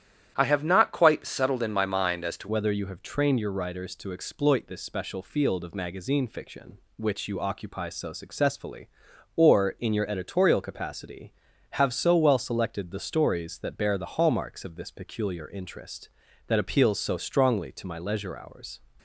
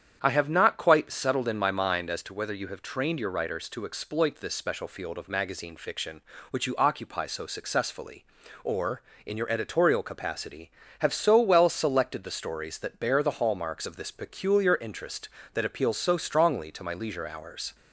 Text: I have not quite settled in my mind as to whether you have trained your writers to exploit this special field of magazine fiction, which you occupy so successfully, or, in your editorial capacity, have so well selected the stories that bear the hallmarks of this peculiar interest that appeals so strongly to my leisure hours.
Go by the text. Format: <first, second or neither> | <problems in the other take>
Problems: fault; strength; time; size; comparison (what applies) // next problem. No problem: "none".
second | starts louder than the rest; strong; until 1.3 s; 10.5 dB; strong in the second // changes voice at "whether"; from 2.4 s on; 16.3 s long